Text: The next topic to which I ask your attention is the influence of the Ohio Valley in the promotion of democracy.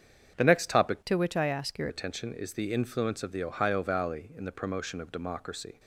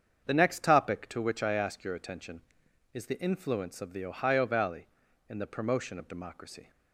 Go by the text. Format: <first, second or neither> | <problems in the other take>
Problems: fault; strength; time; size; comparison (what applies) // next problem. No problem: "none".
second | starts louder than the rest; strong; until 1.3 s; 7.5 dB; strong in the second // changes voice from "to" to "your"; from 1.0 to 1.8 s; 0.8 s long